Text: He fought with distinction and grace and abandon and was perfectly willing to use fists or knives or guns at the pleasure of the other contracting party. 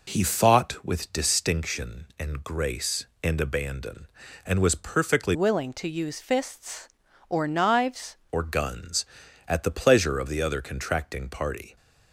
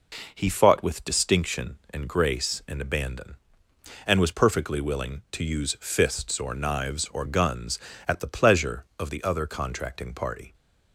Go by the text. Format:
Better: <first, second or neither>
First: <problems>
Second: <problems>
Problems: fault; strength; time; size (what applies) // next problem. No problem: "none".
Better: second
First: changes voice from "willing" to "knives"; from 5.3 to 8.1 s; 2.8 s long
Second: none